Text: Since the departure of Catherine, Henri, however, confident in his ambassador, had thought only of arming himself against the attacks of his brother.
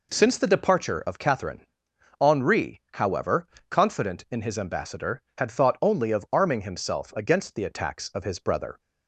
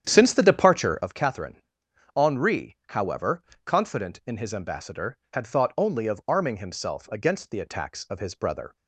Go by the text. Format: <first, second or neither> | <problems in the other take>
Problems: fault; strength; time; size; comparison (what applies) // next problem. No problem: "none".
first | starts louder than the rest; strong; until 1.2 s; 9.5 dB